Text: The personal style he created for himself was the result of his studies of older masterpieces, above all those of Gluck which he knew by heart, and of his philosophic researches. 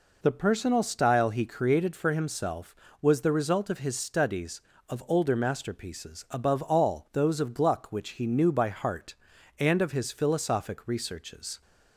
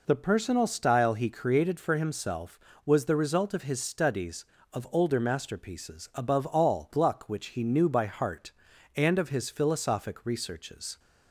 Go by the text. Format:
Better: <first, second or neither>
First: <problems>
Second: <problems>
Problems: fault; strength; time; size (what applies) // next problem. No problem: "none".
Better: first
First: none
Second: skips "those of"; at 6.9 s